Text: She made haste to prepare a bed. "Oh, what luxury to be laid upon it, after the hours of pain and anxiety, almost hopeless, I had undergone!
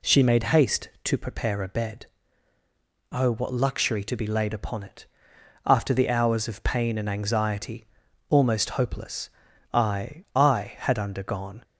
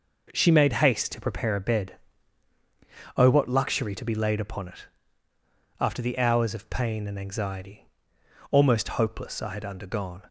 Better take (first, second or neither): second